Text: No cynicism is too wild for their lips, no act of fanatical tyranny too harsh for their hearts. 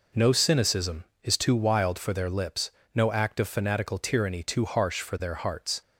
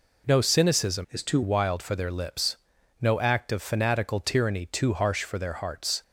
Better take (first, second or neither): first